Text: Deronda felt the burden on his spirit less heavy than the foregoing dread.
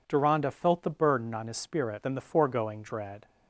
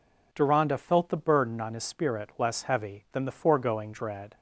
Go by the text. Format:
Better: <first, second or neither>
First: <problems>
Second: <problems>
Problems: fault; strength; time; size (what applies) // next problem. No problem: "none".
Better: second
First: skips "less heavy"; at 2.0 s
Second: none